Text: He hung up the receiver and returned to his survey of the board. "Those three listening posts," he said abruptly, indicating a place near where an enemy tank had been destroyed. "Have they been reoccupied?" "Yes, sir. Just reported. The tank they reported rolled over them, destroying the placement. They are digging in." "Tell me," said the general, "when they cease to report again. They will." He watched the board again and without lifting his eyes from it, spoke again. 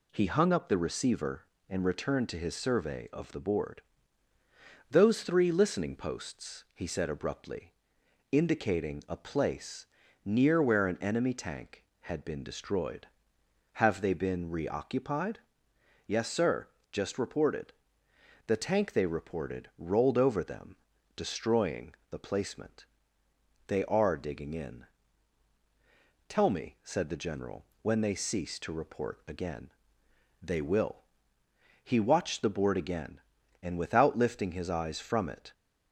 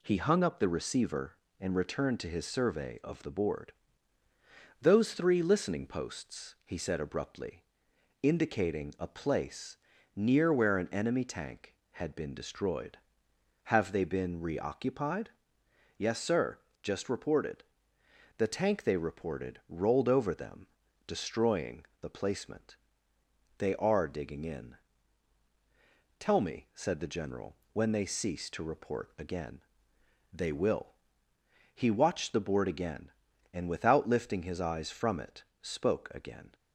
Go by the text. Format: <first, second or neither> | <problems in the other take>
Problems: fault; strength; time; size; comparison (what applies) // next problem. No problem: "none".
second | pauses between "place" and "near"; at 9.8 s; 0.38 s long; also in the second // stops before "spoke again"; at 35.5 s